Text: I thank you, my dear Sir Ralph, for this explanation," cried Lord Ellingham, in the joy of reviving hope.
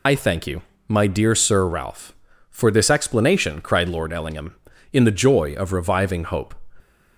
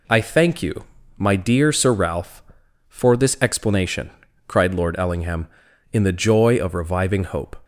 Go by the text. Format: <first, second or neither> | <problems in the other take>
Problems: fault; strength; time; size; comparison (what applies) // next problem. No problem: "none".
second | loses the start of "I"; at 0.0 s; 70 ms